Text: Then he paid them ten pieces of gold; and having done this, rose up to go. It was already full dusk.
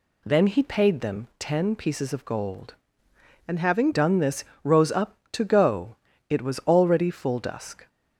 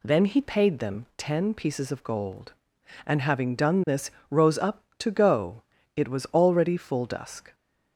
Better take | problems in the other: second | changes voice from "and" to "having"; from 3.4 to 3.9 s; 0.5 s long

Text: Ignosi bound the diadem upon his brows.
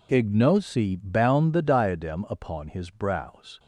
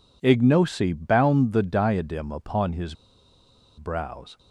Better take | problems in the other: first | pauses between "his" and "brows"; noticeable; at 2.9 s; 0.83 s long

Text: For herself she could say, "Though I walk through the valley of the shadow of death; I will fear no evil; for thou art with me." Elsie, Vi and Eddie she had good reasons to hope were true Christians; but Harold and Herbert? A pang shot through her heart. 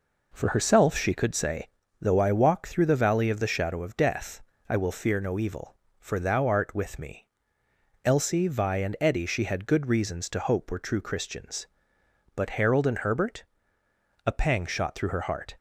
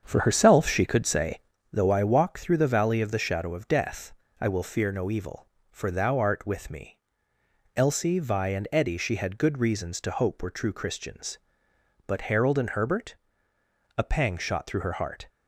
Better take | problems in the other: first | starts louder than the rest; strong; until 1.8 s; 7.5 dB

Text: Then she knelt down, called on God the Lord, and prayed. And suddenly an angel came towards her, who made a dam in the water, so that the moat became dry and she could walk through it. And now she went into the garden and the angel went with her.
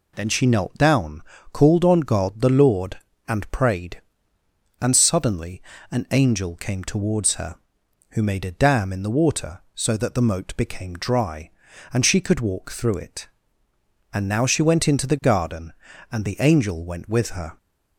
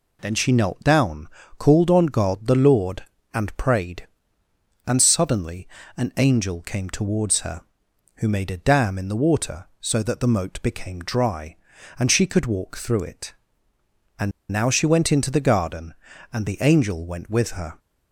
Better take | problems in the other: first | pauses between "suddenly" and "an"; slight; at 5.6 s; 0.28 s long; slight in the first // pauses between "And" and "now"; slight; at 14.3 s; 0.21 s long

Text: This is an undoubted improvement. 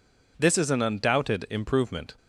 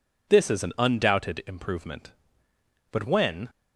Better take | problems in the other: first | goes on to say "But when"; from 2.8 s on; 0.60 s long

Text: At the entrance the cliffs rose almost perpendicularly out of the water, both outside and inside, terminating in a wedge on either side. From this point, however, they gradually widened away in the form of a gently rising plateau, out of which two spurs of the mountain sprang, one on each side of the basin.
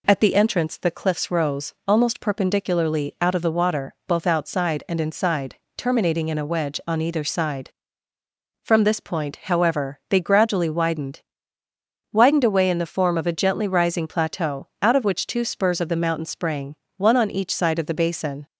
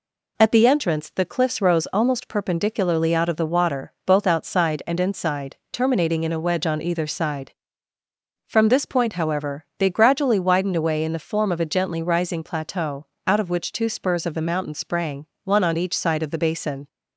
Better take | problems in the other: second | says "widened" twice; at 12.1 s

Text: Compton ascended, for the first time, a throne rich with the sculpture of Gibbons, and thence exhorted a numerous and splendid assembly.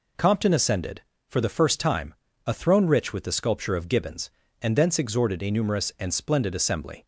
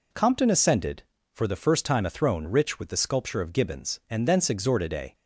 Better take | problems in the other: first | stops before "numerous and splendid assembly"; at 5.1 s

